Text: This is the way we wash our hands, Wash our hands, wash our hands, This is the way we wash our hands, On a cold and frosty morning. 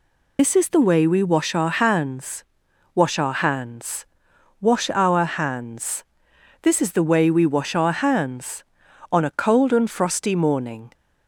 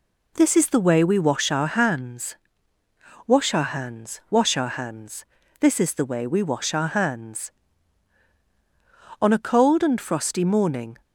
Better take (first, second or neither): second